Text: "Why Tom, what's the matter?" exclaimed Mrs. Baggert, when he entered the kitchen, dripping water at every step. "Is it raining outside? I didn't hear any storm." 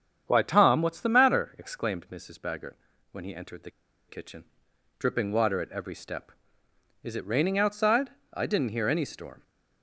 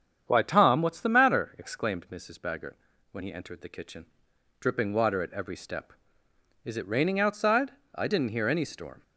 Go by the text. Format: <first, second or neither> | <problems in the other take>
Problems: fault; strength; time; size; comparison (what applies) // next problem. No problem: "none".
second | starts louder than the rest; strong; until 1.2 s; 8 dB; strong in the second // pauses between "the" and "kitchen"; at 3.6 s; 0.38 s long